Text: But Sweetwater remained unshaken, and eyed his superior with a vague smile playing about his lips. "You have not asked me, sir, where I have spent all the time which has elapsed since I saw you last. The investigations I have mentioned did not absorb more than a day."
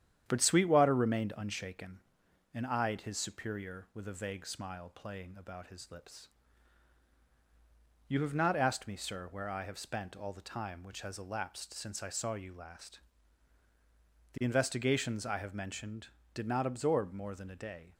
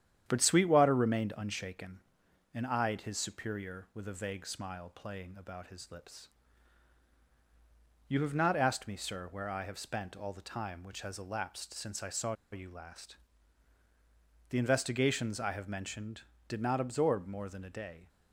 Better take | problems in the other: first | starts louder than the rest; strong; until 1.2 s; 9.5 dB; strong in the first // pauses between "saw" and "you"; slight; at 12.3 s; 0.18 s long

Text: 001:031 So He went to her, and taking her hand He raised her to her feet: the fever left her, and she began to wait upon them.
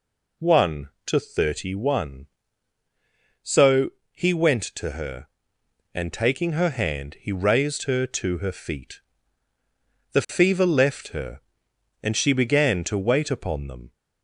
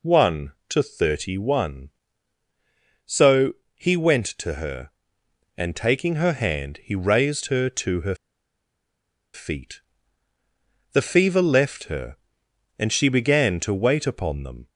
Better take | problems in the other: first | pauses between "So" and "He"; slight; at 3.5 s; 0.22 s long; slight in the first // pauses between "her" and "feet"; at 8.1 s; 1.1 s long

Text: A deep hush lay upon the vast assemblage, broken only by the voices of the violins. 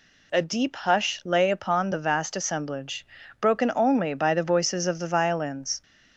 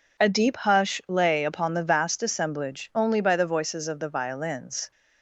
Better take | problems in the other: first | skips "broken"; at 2.9 s

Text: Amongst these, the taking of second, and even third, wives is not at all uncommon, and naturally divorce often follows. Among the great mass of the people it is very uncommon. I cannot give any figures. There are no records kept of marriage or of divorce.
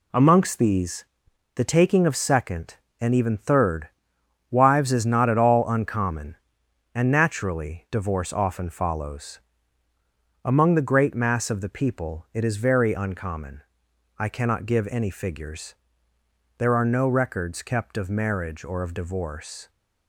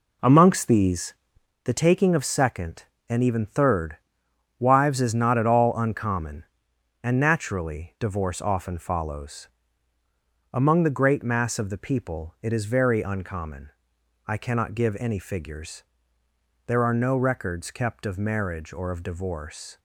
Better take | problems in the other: first | starts louder than the rest; until 1.6 s; 3.5 dB

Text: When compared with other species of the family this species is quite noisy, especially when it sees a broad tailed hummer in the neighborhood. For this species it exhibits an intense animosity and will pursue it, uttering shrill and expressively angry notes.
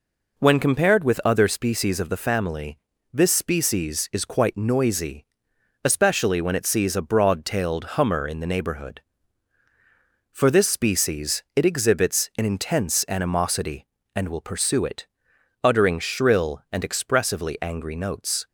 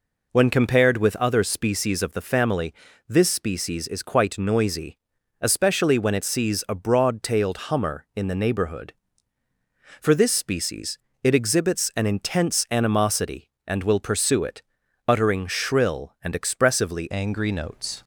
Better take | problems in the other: first | pauses between "family" and "this"; slight; at 2.7 s; 0.36 s long; slight in the first // pauses between "species" and "it"; slight; at 10.9 s; 0.24 s long // changes voice at "angry"; from 17.1 s on; 0.9 s long

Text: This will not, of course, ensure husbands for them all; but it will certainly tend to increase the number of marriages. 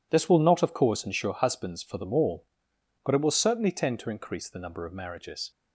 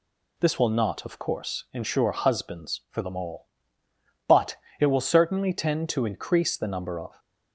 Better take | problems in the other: first | pauses between "but" and "it"; slight; at 4.5 s; 0.22 s long // stops before "marriages"; at 7.1 s

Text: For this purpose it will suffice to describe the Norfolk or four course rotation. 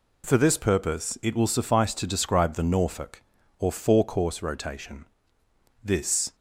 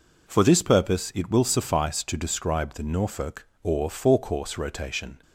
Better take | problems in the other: second | goes on to say "This"; from 5.8 s on; 0.52 s long

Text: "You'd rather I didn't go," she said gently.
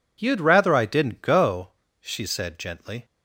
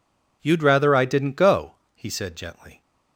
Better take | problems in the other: first | says "he" for "she"; at 1.9 s

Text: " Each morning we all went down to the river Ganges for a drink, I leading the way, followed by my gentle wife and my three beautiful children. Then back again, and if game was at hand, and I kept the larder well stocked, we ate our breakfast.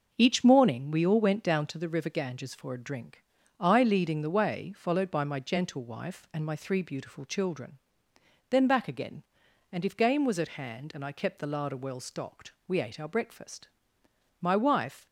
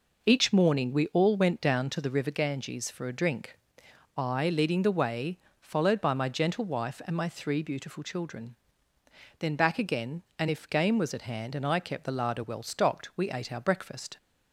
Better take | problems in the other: second | goes on to say "My wife"; noticeable; from 14.4 s on; 0.66 s long

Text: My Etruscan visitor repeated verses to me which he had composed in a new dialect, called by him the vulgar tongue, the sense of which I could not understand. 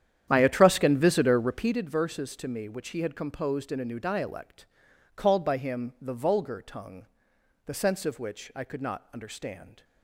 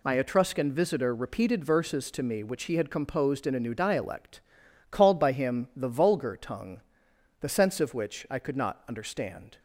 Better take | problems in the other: second | starts louder than the rest; strong; until 1.8 s; 10 dB

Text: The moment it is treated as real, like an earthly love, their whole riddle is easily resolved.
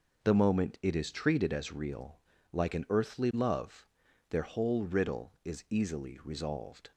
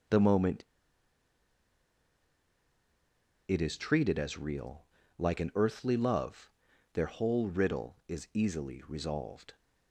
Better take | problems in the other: first | pauses between "moment" and "it"; strong; at 0.6 s; 2.8 s long

